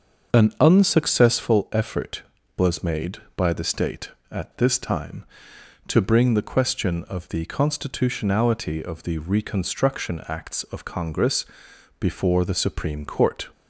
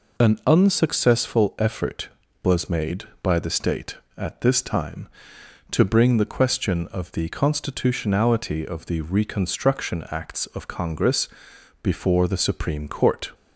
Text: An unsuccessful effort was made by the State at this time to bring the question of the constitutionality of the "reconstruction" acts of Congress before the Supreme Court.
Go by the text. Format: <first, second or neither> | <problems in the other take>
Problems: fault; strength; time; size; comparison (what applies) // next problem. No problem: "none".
second | starts louder than the rest; until 1.6 s; 6.5 dB // pauses between "Congress" and "before"; noticeable; at 11.4 s; 0.54 s long; noticeable in the second